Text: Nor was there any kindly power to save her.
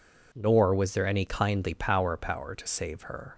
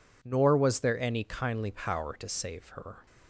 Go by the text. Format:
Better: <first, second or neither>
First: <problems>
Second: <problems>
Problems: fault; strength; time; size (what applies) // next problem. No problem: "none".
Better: second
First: says "power" twice; at 2.1 s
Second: none